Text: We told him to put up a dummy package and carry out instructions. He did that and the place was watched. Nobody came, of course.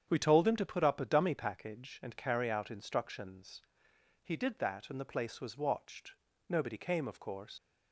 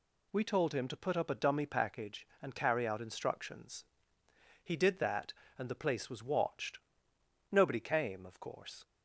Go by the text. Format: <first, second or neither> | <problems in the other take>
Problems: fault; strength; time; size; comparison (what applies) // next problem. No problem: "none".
second | starts louder than the rest; strong; until 1.0 s; 8.5 dB // leaves "course" unfinished; at 7.5 s; 90 ms